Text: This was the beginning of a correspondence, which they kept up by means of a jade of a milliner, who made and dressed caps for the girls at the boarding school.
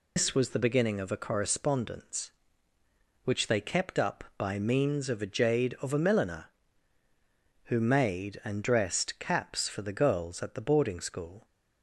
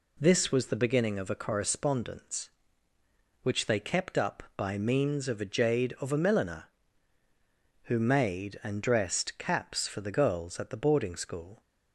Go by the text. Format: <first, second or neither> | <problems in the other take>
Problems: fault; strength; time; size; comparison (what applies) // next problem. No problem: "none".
second | loses the start of "This"; at 0.1 s; 160 ms